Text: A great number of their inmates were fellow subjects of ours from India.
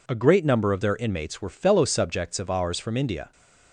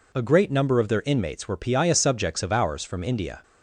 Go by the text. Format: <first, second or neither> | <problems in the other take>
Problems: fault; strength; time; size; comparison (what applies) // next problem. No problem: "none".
first | says "piaya" for "fellow"; at 1.5 s